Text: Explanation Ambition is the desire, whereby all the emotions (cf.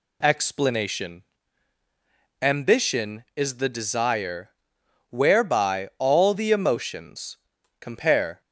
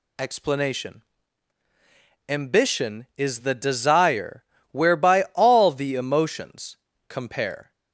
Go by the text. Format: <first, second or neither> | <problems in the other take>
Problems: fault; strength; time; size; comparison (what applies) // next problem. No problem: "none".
neither | pauses between "Explanation" and "Ambition"; the same in both